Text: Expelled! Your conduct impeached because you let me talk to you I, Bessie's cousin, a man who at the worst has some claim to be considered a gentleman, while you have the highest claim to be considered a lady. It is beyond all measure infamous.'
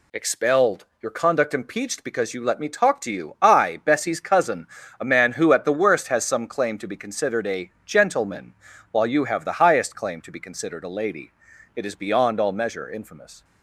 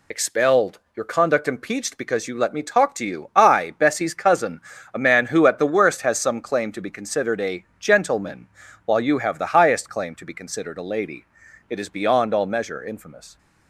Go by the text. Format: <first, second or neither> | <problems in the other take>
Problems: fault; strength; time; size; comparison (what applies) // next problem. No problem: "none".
first | loses the start of "Expelled"; at 0.1 s; 50 ms // pauses between "a" and "gentleman"; slight; at 7.6 s; 0.16 s long; slight in the first